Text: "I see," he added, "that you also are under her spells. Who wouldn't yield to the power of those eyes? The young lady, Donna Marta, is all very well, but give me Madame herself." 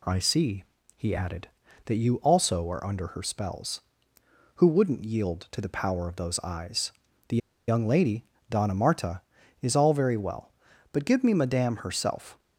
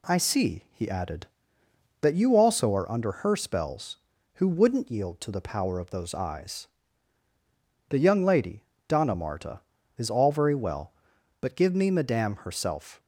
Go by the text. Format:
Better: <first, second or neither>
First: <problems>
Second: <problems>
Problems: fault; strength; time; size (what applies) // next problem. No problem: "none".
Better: second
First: pauses between "The" and "young"; slight; at 7.3 s; 0.30 s long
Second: none